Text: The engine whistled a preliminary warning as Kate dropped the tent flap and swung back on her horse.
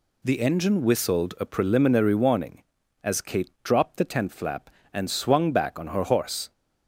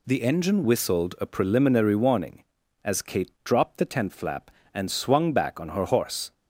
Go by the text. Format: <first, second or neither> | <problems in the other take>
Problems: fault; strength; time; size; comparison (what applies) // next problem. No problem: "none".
neither | none